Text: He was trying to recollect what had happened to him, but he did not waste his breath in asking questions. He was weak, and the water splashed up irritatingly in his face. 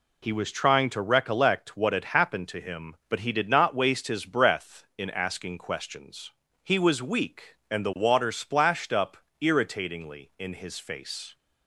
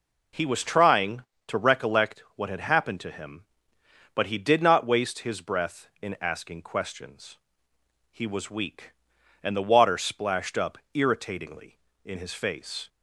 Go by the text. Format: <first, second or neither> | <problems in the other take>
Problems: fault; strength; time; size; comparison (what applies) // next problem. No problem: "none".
neither | pauses between "up" and "irritatingly"; slight; the same in both